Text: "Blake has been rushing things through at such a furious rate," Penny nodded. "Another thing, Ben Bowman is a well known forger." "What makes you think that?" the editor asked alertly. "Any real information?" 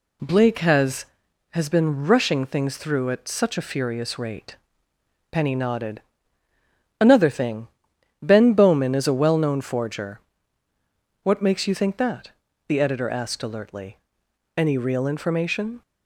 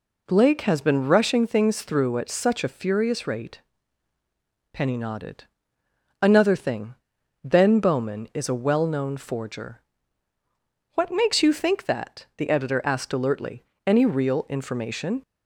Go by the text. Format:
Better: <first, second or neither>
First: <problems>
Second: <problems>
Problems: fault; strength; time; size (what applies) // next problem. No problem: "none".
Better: second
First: says "has" twice; at 1.5 s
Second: none